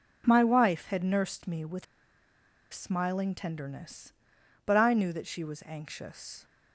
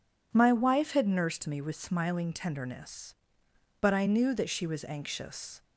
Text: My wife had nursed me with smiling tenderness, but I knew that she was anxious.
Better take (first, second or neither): second